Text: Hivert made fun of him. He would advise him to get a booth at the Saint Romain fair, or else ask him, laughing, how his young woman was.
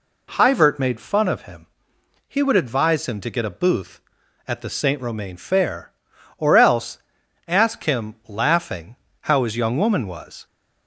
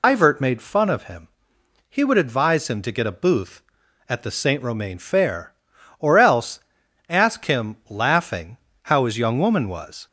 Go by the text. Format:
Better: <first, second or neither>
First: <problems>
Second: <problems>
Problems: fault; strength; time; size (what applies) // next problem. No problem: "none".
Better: first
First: pauses between "else" and "ask"; noticeable; at 6.9 s; 0.48 s long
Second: loses the start of "Hivert"; at 0.0 s; 140 ms // pauses between "else" and "ask"; noticeable; at 6.6 s; 0.48 s long